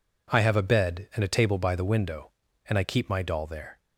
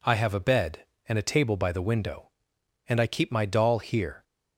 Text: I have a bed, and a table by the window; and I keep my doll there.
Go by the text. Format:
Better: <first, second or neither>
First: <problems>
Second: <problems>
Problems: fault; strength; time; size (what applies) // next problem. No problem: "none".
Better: first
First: none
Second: says "here" for "there"; at 3.7 s